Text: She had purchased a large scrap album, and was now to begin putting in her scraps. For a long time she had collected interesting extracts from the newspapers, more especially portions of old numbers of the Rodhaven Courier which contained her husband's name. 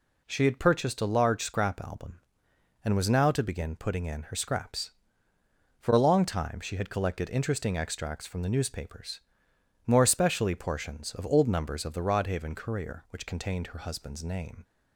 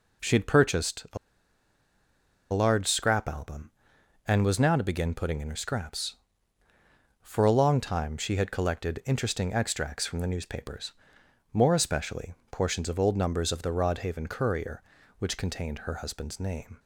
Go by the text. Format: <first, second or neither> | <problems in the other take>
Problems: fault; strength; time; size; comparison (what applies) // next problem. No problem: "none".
first | pauses between "a" and "large"; strong; at 1.1 s; 1.3 s long // pauses between "especially" and "portions"; slight; at 12.3 s; 0.18 s long